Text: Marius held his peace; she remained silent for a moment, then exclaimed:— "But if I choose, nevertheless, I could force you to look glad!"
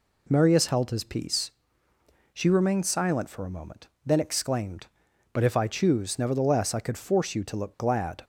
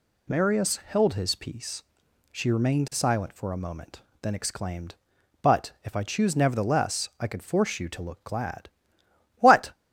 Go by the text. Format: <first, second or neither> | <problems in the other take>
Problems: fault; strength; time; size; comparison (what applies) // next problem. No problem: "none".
first | goes on to say "What"; slight; from 9.3 s on; 0.34 s long